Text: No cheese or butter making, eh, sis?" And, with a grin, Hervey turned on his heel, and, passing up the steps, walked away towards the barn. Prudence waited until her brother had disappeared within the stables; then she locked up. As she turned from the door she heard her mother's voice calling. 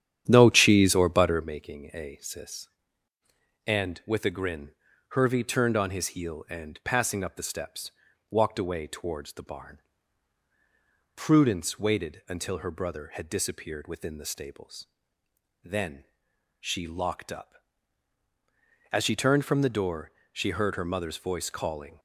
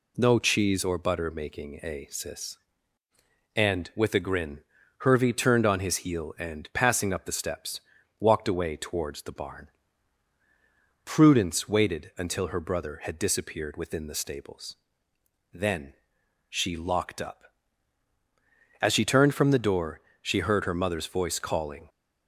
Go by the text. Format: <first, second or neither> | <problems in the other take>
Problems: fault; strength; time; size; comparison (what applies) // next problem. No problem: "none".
second | starts louder than the rest; strong; until 1.6 s; 10 dB // pauses between "then" and "she"; noticeable; at 16.0 s; 0.54 s long; noticeable in the second // pauses between "door" and "she"; slight; at 20.0 s; 0.24 s long; slight in the second